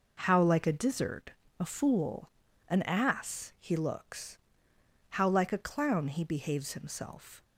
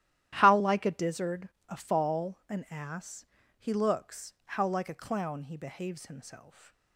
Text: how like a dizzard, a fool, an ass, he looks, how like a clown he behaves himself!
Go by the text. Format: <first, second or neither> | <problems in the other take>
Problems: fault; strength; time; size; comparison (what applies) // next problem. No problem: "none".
first | starts louder than the rest; strong; until 1.4 s; 12.5 dB // says "fall" for "fool"; at 1.7 s